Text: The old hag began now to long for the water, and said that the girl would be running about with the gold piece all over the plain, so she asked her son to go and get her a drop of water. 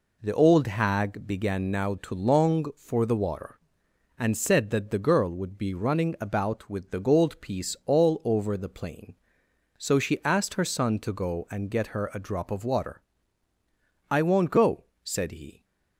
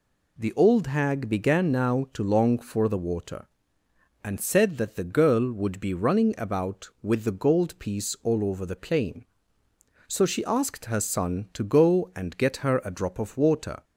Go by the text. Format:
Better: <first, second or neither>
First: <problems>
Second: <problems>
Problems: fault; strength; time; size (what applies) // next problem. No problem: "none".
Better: second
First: goes on to say "I won't go said he"; from 14.1 s on; 1.5 s long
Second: none